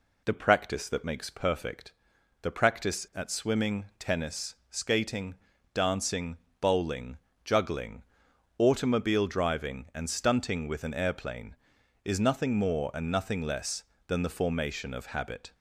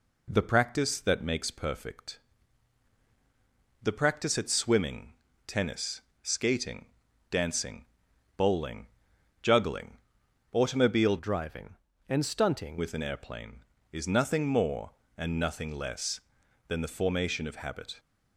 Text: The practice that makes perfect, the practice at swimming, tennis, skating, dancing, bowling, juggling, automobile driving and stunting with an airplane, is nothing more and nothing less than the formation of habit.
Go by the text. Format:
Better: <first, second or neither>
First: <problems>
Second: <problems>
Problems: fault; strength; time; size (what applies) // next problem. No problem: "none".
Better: first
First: none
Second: changes voice from "driving" to "stunting"; from 11.1 to 12.7 s; 1.6 s long